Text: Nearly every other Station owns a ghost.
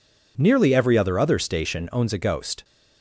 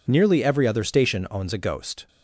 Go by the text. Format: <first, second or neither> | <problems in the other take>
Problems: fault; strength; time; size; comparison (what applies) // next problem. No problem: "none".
second | says "other" twice; at 1.1 s